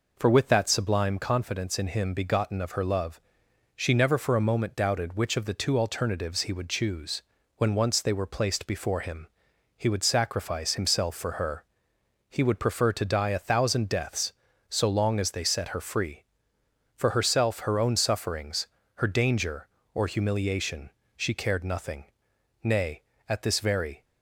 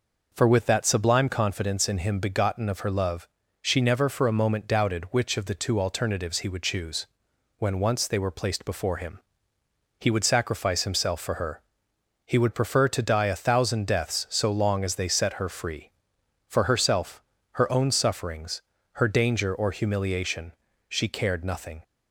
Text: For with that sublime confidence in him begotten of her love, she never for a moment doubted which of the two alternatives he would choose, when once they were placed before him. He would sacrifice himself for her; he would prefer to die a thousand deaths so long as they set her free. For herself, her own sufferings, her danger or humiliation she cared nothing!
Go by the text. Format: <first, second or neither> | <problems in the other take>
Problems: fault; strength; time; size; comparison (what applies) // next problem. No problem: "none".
second | pauses between "humiliation" and "she"; slight; at 20.8 s; 0.26 s long; slight in the second // goes on to say "Nay at this very"; from 22.6 s on; 1.4 s long